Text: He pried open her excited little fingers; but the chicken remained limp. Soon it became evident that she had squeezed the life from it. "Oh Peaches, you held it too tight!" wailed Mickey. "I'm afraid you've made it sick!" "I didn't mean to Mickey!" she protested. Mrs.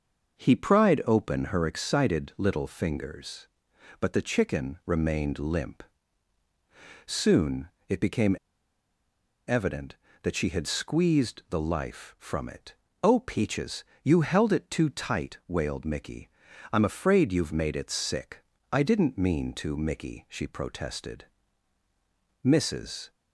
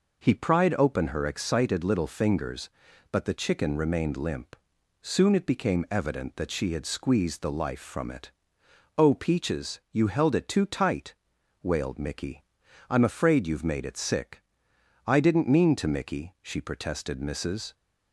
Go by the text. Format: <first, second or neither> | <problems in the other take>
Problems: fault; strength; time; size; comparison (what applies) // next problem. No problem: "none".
second | starts louder than the rest; noticeable; until 1.4 s; 6 dB // pauses between "Soon" and "it"; slight; at 7.6 s; 0.20 s long // pauses between "became" and "evident"; at 8.3 s; 1.0 s long